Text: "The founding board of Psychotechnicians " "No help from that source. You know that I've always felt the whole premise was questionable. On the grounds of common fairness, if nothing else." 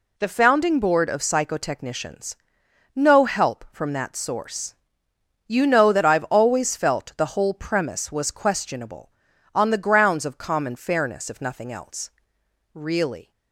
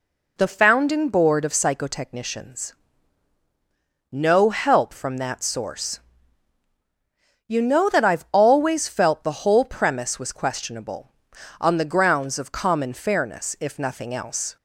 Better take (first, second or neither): second